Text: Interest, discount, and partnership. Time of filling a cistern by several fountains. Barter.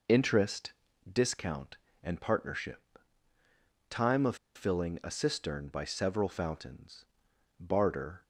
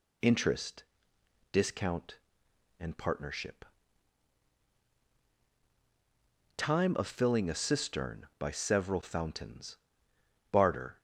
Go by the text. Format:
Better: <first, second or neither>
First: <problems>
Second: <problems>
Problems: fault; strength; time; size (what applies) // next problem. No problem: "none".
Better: second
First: pauses between "of" and "filling"; slight; at 4.3 s; 0.20 s long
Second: none